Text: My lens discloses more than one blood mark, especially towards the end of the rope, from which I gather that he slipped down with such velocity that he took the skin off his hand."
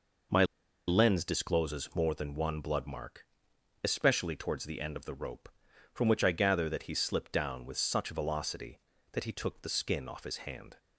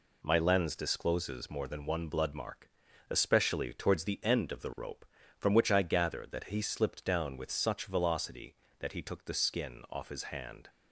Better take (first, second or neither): second